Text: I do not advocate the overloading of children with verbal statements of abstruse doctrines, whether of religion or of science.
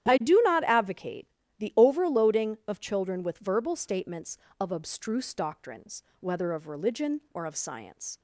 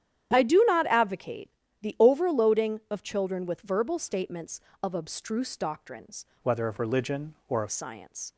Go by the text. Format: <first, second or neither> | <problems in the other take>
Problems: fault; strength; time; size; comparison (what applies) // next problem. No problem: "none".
first | starts louder than the rest; strong; until 1.3 s; 10.5 dB; strong in the first // pauses between "advocate" and "the"; slight; at 1.4 s; 0.32 s long; slight in the first // changes voice from "whether" to "of"; from 6.4 to 7.6 s; 1.2 s long